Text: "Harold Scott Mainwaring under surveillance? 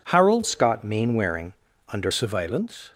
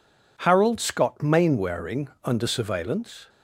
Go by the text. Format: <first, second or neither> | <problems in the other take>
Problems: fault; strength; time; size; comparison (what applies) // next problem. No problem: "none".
second | changes voice from "Scott" to "under"; from 0.4 to 2.1 s; 1.7 s long // pauses between "Mainwaring" and "under"; at 1.5 s; 0.40 s long